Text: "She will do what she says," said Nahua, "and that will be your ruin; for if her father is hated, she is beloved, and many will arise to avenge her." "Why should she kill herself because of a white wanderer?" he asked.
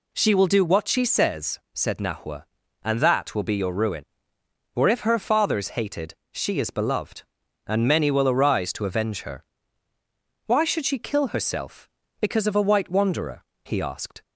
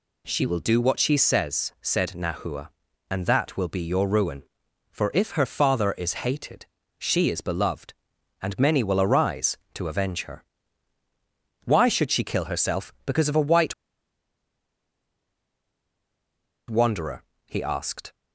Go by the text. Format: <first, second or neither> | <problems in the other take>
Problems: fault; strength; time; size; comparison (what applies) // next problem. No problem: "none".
first | pauses between "white" and "wanderer"; strong; at 13.7 s; 2.9 s long